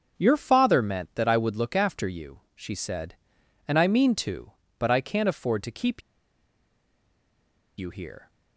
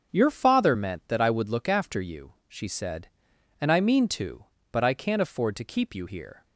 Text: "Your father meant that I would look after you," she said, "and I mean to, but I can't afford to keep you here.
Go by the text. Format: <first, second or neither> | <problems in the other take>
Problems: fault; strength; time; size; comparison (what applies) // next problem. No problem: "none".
second | starts louder than the rest; until 1.2 s; 7 dB; also in the second // pauses between "keep" and "you"; strong; at 6.0 s; 1.7 s long